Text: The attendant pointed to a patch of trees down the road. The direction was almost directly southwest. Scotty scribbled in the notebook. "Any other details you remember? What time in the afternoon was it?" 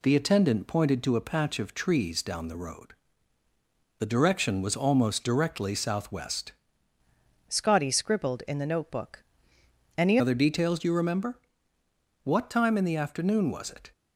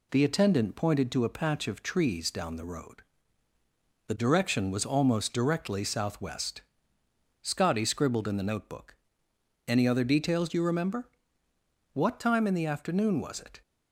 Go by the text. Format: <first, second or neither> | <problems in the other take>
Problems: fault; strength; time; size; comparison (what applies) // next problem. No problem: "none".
second | changes voice from "Scotty" to "Any"; from 7.4 to 10.1 s; 2.7 s long